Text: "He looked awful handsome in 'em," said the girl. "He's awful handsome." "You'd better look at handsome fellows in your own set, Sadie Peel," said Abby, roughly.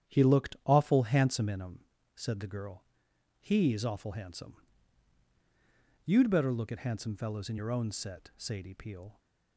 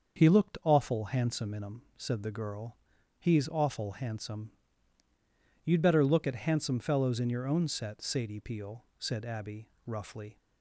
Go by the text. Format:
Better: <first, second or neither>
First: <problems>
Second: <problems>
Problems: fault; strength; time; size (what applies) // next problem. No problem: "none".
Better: second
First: starts louder than the rest; strong; until 1.1 s; 9.5 dB // stops before "said Abby roughly"; at 9.1 s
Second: starts louder than the rest; until 1.2 s; 6.5 dB